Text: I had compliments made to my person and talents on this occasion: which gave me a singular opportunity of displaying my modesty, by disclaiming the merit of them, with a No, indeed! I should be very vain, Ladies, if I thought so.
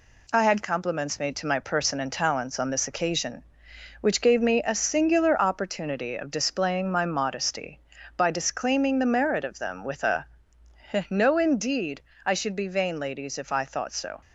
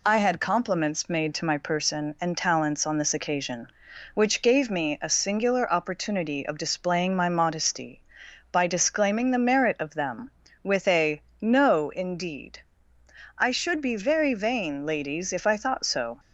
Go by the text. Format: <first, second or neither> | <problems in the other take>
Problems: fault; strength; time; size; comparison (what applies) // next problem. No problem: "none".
second | pauses between "a" and "No"; noticeable; at 10.2 s; 0.82 s long; slight in the second // skips "very"; at 12.6 s